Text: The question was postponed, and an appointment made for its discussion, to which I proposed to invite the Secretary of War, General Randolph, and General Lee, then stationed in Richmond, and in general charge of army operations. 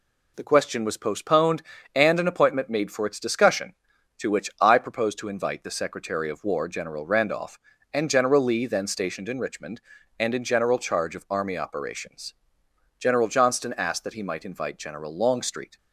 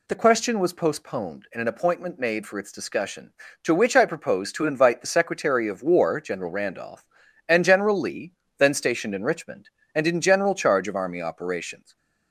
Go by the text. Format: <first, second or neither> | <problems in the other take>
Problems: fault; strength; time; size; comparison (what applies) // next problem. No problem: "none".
second | goes on to say "General Johnston asked that he might invite General Longstreet"; strong; from 12.9 s on; 2.7 s long